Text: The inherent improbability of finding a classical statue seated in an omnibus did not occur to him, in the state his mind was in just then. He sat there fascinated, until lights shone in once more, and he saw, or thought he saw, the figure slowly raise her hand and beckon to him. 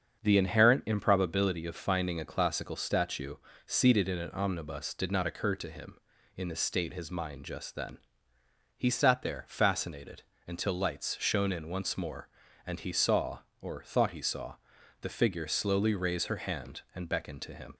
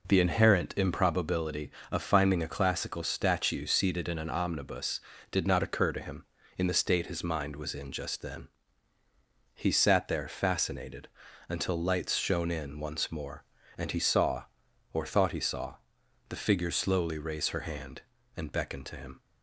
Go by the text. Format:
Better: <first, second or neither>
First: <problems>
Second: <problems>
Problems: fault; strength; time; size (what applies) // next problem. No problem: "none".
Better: second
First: starts louder than the rest; until 1.2 s; 7 dB // pauses between "statue" and "seated"; slight; at 3.3 s; 0.28 s long // skips "was in"; at 7.4 s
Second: none